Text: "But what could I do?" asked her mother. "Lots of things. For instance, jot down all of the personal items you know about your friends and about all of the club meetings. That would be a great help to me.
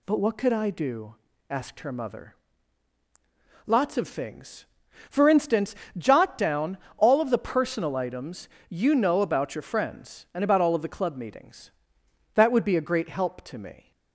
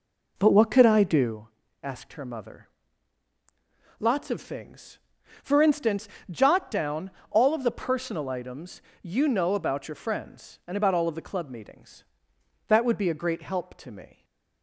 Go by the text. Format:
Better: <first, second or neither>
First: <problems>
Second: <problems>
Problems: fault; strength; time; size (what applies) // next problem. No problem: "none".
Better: first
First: pauses between "down" and "all"; slight; at 6.7 s; 0.20 s long // pauses between "items" and "you"; slight; at 8.4 s; 0.22 s long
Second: starts louder than the rest; noticeable; until 1.4 s; 4 dB // pauses between "down" and "all"; slight; at 7.0 s; 0.20 s long // pauses between "items" and "you"; slight; at 8.7 s; 0.22 s long // stays silent after the last word; slight; from 14.1 s on; 0.5 s long